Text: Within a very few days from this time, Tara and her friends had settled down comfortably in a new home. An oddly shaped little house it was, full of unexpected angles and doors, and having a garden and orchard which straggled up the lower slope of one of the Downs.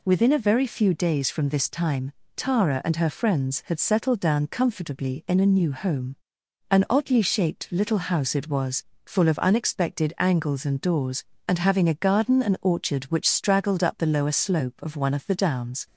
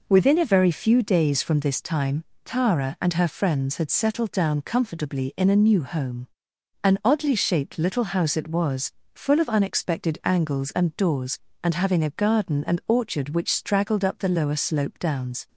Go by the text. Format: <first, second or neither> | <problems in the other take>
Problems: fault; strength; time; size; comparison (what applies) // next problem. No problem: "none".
first | skips "of one of the"; at 14.9 s